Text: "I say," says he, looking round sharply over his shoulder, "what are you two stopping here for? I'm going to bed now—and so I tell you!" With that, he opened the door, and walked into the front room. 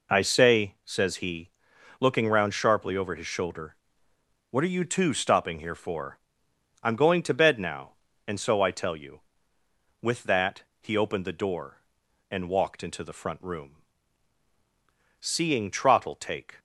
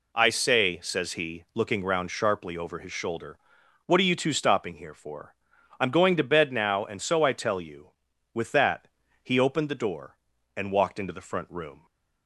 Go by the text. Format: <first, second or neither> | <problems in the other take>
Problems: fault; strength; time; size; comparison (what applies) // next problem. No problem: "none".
second | goes on to say "Seeing Trottle take"; from 15.1 s on; 1.4 s long